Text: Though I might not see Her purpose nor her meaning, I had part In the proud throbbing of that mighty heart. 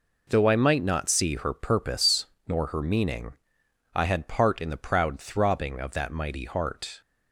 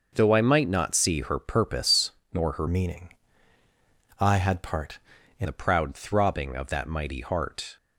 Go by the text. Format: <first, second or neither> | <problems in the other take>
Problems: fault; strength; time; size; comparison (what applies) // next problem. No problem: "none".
first | pauses between "purpose" and "nor"; slight; at 2.1 s; 0.20 s long; slight in the first // changes voice from "meaning" to "In"; from 2.6 to 5.4 s; 2.8 s long